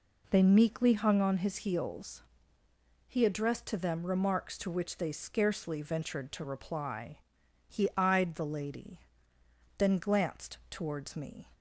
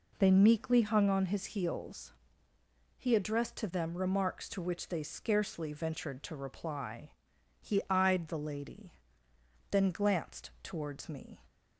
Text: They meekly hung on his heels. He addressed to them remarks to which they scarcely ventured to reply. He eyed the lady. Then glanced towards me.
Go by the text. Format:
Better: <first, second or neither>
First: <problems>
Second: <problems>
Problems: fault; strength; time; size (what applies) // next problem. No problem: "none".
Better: neither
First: none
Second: none